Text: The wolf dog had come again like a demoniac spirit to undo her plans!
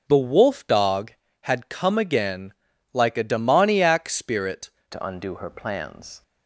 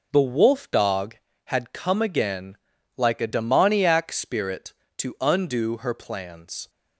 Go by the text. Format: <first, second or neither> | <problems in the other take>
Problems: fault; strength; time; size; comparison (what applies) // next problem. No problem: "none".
second | starts louder than the rest; until 1.1 s; 6 dB // pauses between "again" and "like"; at 2.5 s; 0.40 s long; also in the second // changes voice at "to"; from 4.9 s on; 1.3 s long